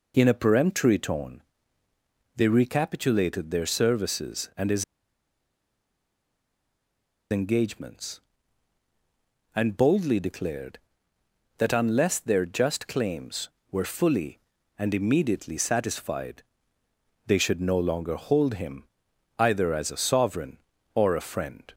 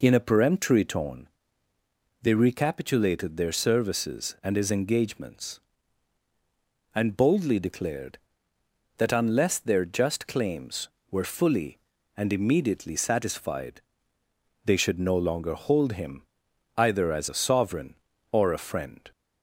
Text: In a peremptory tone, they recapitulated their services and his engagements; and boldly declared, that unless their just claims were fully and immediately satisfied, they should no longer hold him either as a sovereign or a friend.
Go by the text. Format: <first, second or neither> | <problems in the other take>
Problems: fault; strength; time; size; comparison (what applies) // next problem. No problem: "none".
second | pauses between "his" and "engagements"; strong; at 4.8 s; 2.4 s long // pauses between "him" and "either"; noticeable; at 18.8 s; 0.56 s long; noticeable in the second